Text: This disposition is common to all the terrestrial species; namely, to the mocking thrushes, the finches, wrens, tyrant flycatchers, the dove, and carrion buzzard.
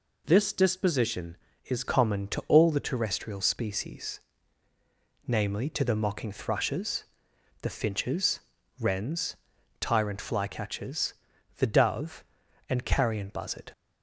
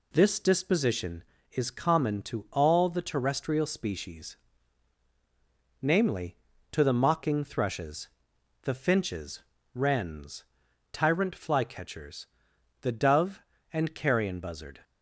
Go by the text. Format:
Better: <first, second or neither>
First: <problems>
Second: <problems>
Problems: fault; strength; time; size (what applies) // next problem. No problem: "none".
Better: second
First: changes voice at "common"; from 1.8 s on; 11.9 s long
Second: none